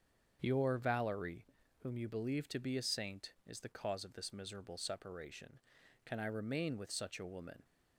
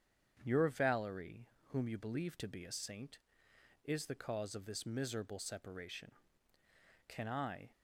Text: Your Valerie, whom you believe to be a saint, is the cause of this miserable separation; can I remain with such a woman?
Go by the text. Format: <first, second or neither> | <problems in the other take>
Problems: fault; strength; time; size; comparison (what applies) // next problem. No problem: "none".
first | starts louder than the rest; strong; until 1.4 s; 8 dB; strong in the first // stops before "remain with such a woman"; at 7.7 s